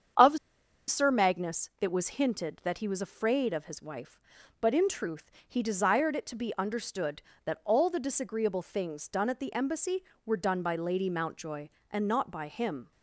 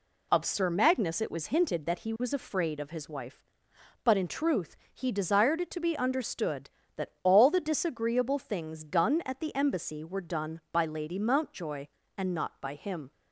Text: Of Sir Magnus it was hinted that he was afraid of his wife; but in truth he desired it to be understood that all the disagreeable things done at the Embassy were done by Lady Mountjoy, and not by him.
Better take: second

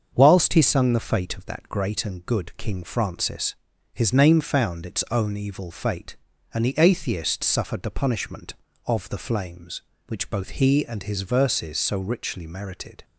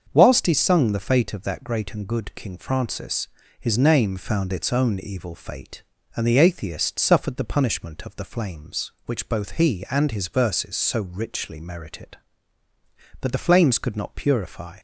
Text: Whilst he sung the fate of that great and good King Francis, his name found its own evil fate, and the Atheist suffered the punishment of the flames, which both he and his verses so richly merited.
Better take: first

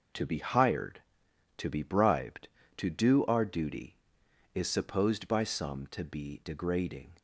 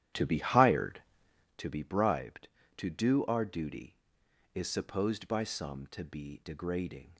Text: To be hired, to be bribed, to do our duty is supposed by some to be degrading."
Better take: first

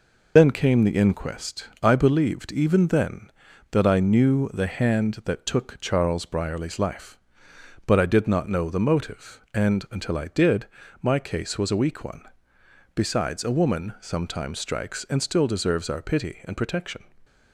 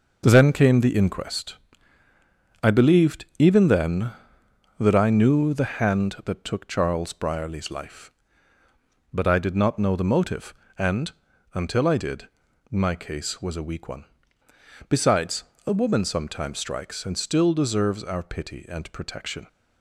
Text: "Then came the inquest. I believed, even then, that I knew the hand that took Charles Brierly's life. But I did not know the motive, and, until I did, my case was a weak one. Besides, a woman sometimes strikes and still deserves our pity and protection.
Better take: second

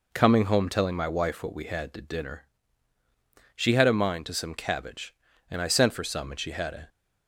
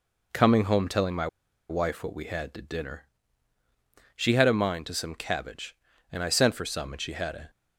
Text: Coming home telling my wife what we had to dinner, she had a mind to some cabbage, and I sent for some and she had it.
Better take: first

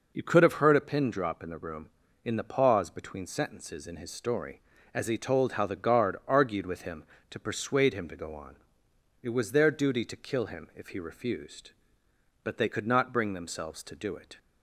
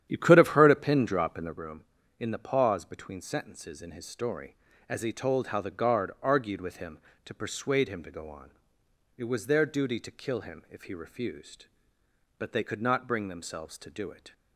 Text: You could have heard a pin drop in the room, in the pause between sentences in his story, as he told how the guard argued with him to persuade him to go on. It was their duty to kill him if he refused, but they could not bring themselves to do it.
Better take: first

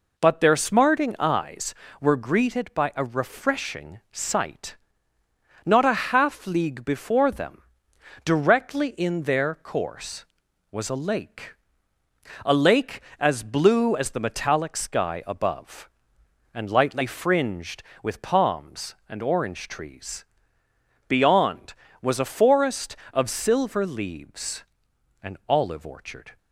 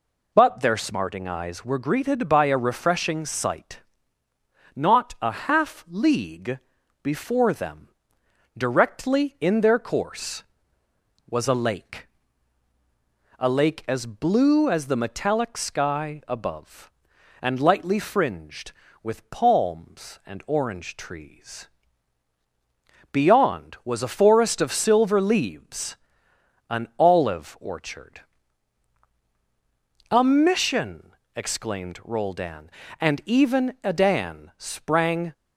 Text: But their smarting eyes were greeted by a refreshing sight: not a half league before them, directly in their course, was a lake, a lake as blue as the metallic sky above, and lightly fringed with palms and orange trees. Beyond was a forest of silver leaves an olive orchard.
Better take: first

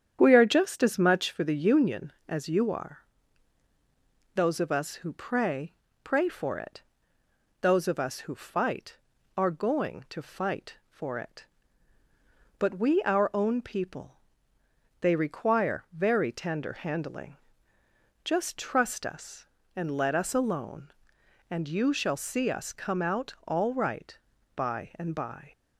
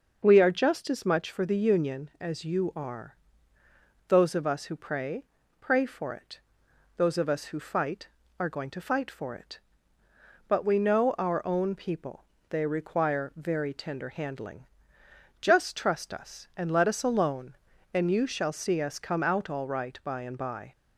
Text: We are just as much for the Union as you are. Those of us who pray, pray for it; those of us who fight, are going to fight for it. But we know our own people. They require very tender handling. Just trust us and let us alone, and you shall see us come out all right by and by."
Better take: second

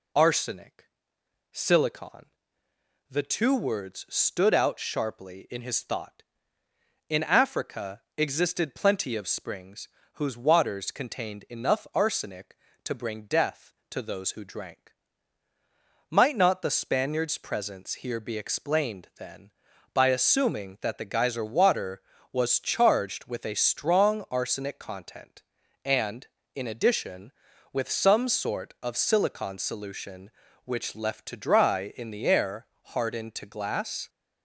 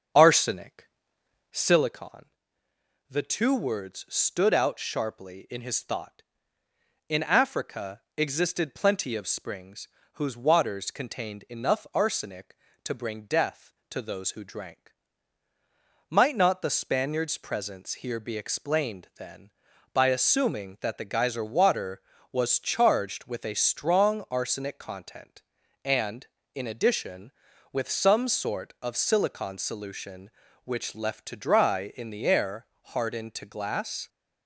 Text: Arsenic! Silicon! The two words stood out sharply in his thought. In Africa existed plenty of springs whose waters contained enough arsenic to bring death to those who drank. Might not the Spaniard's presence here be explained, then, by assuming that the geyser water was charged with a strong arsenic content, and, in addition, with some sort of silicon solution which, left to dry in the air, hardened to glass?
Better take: first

